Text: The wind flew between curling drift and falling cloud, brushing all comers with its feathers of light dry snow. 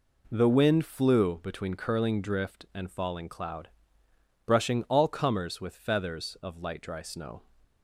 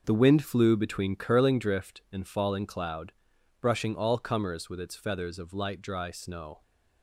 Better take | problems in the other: second | skips "its"; at 5.7 s

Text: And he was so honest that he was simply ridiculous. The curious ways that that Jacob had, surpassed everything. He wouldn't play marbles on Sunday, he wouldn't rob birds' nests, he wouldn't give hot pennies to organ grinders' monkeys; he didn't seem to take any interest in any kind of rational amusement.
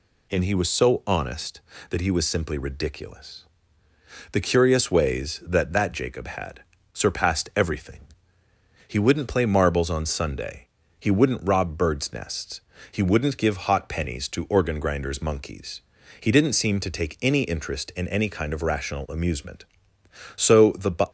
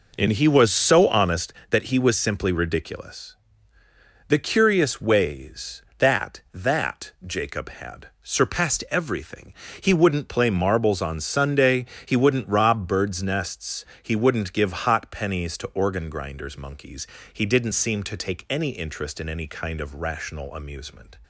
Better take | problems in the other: second | goes on to say "So the"; noticeable; from 20.3 s on; 0.72 s long

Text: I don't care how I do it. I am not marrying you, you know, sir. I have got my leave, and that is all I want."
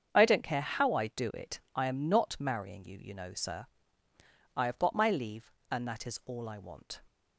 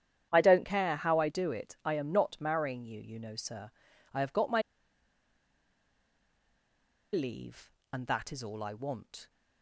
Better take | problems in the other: first | starts louder than the rest; strong; until 1.3 s; 9.5 dB; strong in the first // pauses between "my" and "leave"; strong; at 4.6 s; 2.5 s long

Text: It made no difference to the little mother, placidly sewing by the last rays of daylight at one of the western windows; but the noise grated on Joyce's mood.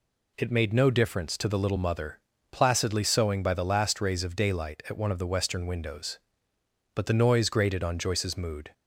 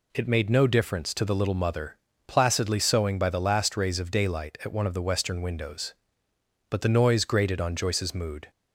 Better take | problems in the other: neither | none

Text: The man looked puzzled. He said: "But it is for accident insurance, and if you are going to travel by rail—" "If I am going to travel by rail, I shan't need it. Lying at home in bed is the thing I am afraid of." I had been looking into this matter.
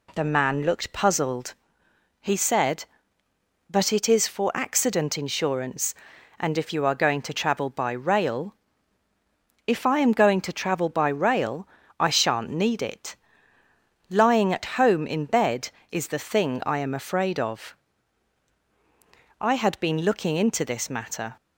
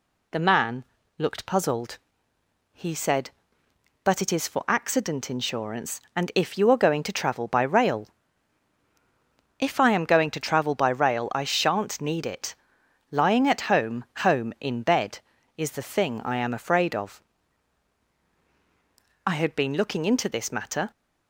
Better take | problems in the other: first | pauses between "man" and "looked"; slight; at 0.8 s; 0.34 s long // says "home" twice; at 14.1 s

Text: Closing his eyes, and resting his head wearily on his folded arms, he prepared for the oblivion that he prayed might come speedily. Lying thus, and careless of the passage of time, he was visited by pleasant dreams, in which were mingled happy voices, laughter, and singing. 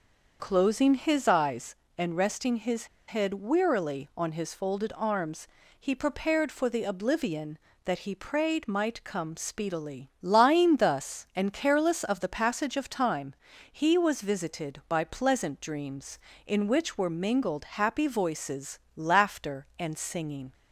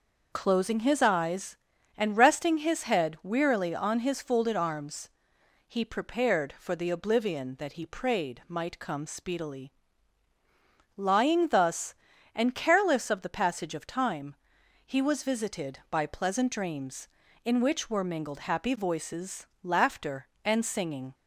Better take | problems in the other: second | starts louder than the rest; until 1.4 s; 6 dB // pauses between "his" and "head"; slight; at 2.8 s; 0.22 s long

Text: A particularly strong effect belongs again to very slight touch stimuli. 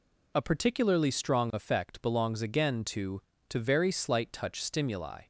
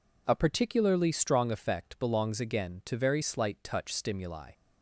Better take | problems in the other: second | says "to" twice; at 3.4 s

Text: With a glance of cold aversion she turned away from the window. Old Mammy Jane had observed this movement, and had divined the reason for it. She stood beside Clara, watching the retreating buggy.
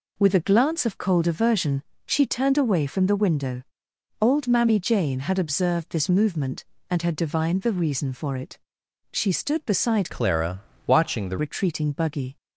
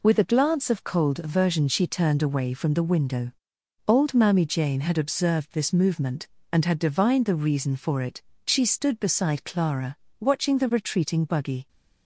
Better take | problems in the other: second | pauses between "aversion" and "she"; slight; at 1.8 s; 0.24 s long // changes voice from "Clara" to "the"; from 10.1 to 11.3 s; 1.2 s long

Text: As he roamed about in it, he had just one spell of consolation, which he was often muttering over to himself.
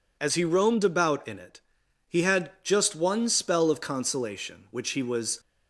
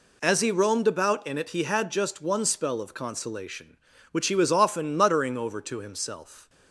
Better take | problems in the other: second | stops before "often muttering over to himself"; at 5.3 s

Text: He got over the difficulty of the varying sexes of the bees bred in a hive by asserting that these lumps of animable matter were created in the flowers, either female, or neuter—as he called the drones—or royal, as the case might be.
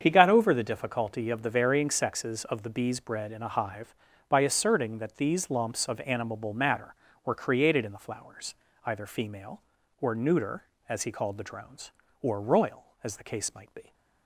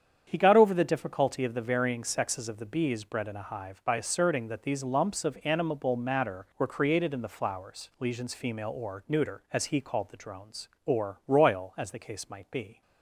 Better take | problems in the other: first | starts louder than the rest; strong; until 1.3 s; 8 dB; strong in the first // says "lesions" for "either"; at 8.0 s

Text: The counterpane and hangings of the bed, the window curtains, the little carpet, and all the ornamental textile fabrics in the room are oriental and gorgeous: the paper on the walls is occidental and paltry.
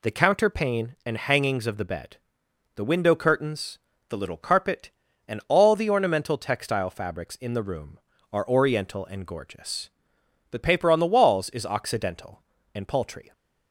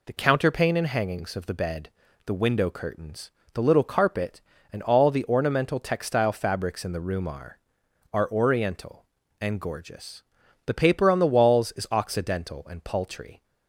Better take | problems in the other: first | says "are" twice; at 8.1 s

